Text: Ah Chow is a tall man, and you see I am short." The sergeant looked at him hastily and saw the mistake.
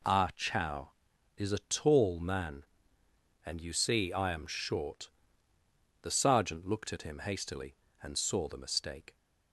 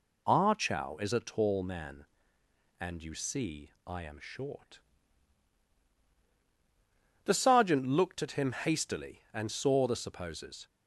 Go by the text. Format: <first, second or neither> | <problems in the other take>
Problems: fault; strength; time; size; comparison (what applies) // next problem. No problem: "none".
first | pauses between "see" and "I"; slight; at 3.7 s; 0.16 s long // says "supposes" for "mistake"; at 9.9 s